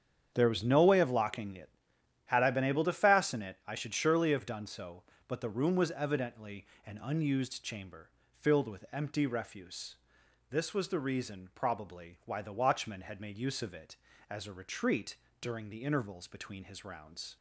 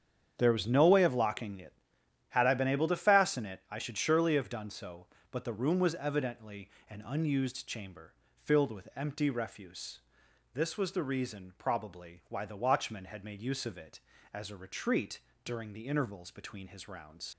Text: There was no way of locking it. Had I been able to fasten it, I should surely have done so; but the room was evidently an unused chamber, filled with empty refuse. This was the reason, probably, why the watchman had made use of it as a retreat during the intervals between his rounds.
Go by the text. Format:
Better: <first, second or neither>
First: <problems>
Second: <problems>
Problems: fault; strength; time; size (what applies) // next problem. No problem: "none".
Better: first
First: starts louder than the rest; strong; until 1.3 s; 8 dB // pauses between "evidently" and "an"; slight; at 6.6 s; 0.22 s long // pauses between "retreat" and "during"; slight; at 15.1 s; 0.26 s long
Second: starts louder than the rest; strong; until 1.3 s; 8 dB // pauses between "evidently" and "an"; slight; at 6.6 s; 0.22 s long // pauses between "retreat" and "during"; slight; at 15.2 s; 0.26 s long // leaves "rounds" unfinished; at 17.3 s; 70 ms